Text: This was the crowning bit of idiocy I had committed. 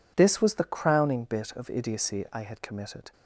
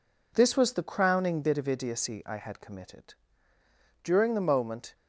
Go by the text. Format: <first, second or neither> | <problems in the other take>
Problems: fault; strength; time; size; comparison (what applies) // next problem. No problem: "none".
first | goes on to say "During the moment"; noticeable; from 4.0 s on; 0.92 s long